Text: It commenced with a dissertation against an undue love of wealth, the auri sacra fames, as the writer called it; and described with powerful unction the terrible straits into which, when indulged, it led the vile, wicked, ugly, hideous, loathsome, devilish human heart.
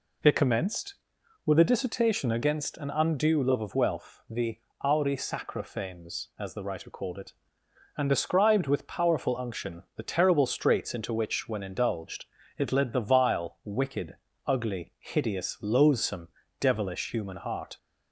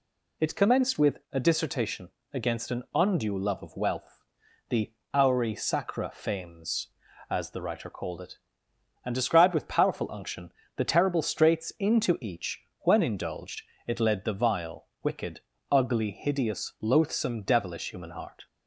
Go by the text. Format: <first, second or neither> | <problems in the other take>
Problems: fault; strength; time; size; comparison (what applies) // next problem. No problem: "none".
first | pauses between "dissertation" and "against"; slight; at 2.0 s; 0.24 s long // pauses between "the" and "auri"; slight; at 4.9 s; 0.22 s long; slight in the first // pauses between "unction" and "the"; slight; at 10.5 s; 0.24 s long // says "each" for "which"; at 12.2 s